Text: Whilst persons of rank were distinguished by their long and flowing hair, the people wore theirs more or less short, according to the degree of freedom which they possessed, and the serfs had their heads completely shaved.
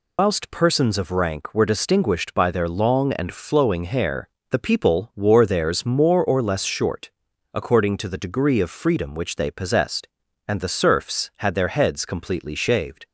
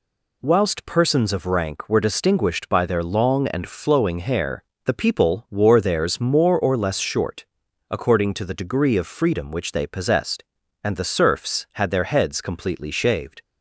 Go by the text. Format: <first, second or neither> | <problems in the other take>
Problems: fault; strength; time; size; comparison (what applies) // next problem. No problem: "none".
second | loses the start of "Whilst"; at 0.1 s; 120 ms